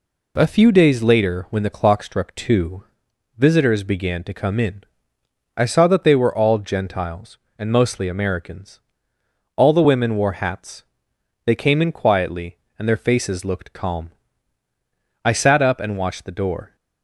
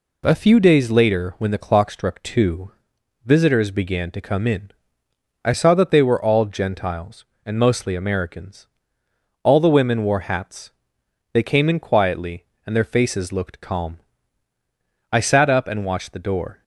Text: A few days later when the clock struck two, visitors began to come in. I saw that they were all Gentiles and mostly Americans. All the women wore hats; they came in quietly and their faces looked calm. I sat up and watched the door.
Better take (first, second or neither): neither